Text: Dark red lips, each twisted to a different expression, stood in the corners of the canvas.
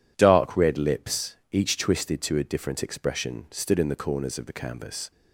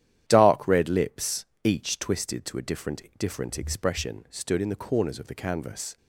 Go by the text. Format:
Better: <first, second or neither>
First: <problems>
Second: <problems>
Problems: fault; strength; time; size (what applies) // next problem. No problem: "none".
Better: first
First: none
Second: starts louder than the rest; strong; until 1.2 s; 11 dB // says "different" twice; at 3.1 s